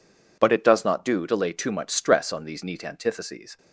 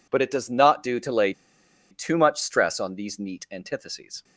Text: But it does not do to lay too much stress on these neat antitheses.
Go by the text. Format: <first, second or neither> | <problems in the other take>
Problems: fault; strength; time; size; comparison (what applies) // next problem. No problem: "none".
first | pauses between "lay" and "too"; noticeable; at 1.3 s; 0.57 s long